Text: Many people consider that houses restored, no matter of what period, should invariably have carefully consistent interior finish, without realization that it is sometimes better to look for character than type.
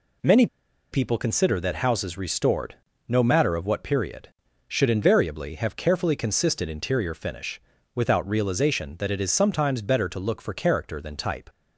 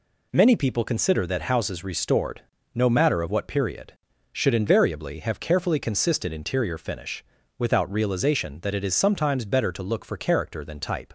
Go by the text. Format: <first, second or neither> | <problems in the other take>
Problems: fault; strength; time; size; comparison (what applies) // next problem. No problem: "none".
second | pauses between "Many" and "people"; noticeable; at 0.4 s; 0.46 s long